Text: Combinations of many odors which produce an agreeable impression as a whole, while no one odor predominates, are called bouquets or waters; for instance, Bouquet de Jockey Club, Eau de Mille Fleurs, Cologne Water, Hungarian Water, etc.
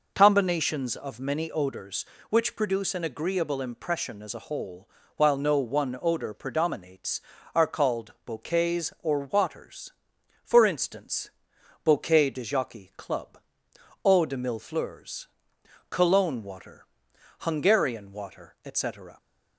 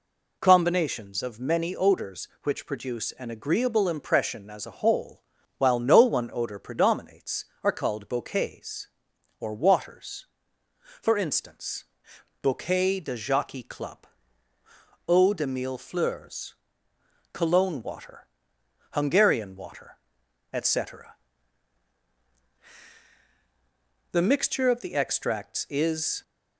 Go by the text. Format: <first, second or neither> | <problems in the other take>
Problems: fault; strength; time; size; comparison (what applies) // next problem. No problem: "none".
first | goes on to say "The mixture of the extracts is"; strong; from 24.1 s on; 2.1 s long